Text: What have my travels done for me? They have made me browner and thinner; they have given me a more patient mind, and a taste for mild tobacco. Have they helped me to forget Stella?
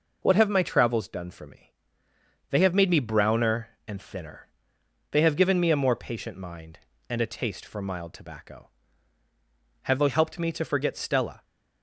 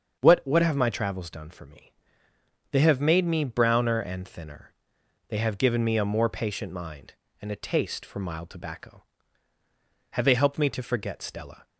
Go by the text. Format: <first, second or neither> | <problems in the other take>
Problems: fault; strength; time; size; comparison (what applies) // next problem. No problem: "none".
first | starts louder than the rest; until 1.2 s; 7 dB // says "What" twice; at 0.4 s